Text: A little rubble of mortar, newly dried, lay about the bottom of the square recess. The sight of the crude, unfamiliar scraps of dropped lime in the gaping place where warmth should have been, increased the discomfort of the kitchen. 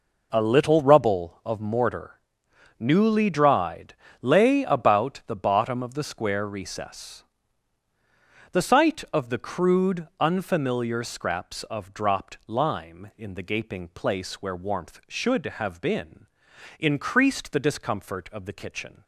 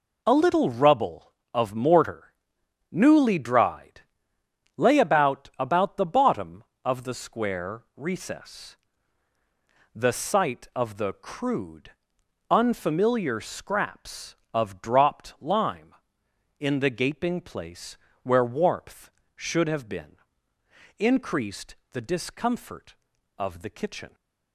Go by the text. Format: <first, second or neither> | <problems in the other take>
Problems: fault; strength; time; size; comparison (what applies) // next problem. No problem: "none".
first | says "about" twice; at 5.5 s // pauses between "place" and "where"; slight; at 17.9 s; 0.26 s long // pauses between "increased" and "the"; slight; at 21.7 s; 0.16 s long